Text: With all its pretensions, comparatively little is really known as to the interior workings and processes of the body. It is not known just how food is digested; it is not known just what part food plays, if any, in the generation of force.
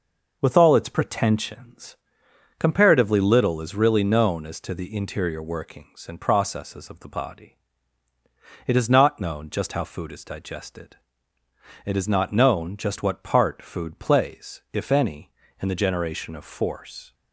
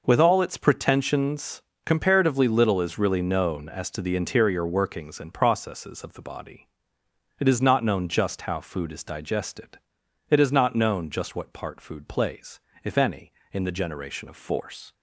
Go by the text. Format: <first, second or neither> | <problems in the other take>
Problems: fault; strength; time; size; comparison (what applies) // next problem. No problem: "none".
neither | none